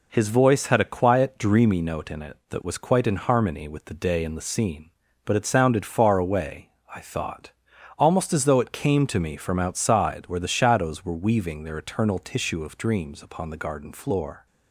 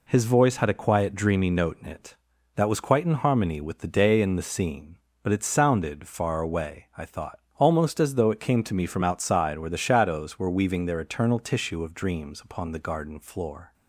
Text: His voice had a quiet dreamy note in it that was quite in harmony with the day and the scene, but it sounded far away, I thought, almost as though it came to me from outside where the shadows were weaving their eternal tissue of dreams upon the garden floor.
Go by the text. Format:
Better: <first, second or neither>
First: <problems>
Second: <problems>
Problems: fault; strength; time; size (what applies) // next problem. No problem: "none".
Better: neither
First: none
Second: none